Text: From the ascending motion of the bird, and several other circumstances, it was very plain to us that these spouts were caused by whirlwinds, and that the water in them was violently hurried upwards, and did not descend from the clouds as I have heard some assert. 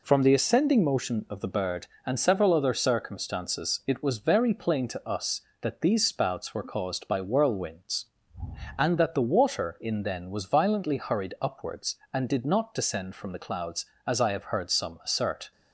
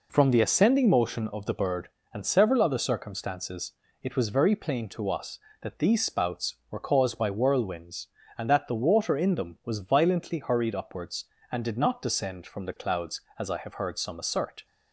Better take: second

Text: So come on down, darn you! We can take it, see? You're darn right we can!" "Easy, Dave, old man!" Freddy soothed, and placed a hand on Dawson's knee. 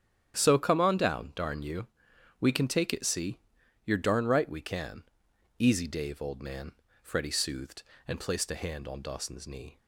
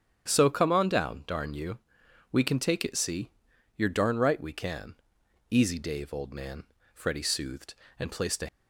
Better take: first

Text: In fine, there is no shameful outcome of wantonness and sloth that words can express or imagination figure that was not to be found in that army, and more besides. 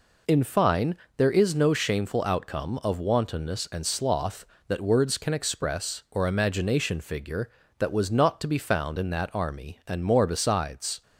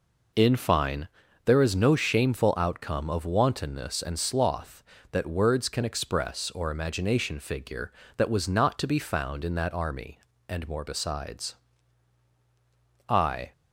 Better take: first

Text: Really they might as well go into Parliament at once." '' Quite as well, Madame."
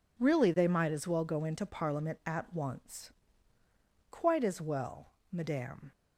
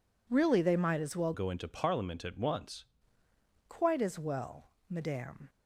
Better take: first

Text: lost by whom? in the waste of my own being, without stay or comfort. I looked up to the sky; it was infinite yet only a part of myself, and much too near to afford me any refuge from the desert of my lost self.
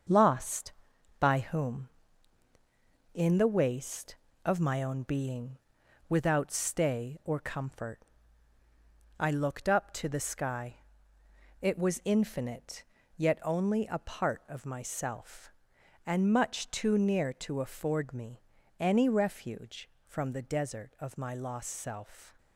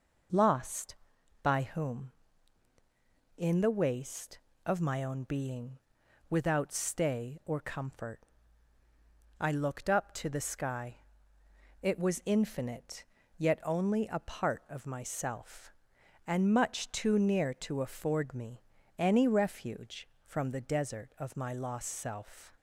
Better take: second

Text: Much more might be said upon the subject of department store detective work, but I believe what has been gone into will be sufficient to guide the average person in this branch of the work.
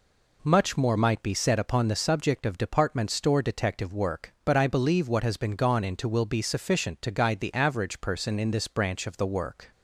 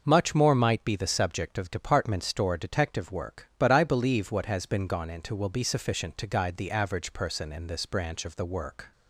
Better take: first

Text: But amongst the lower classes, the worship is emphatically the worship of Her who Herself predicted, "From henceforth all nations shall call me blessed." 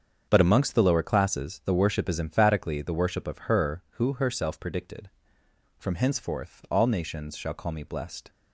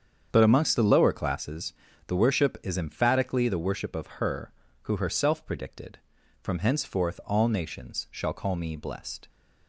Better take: neither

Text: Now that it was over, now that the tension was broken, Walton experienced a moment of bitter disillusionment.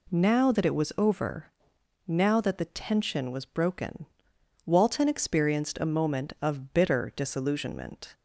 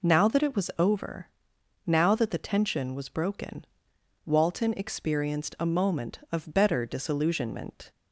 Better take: first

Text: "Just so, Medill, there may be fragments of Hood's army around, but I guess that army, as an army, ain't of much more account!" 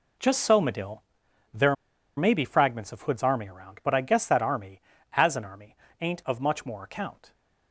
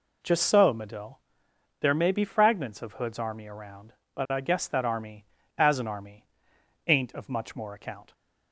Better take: second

